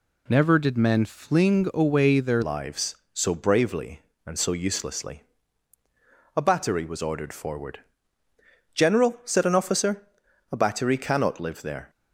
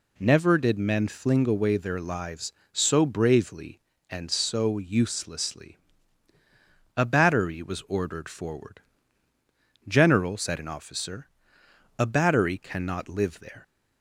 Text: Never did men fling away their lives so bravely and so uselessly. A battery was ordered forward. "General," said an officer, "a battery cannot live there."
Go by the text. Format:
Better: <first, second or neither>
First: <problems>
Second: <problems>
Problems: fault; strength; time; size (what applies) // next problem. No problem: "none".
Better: second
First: changes voice at "lives"; from 2.4 s on; 9.4 s long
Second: none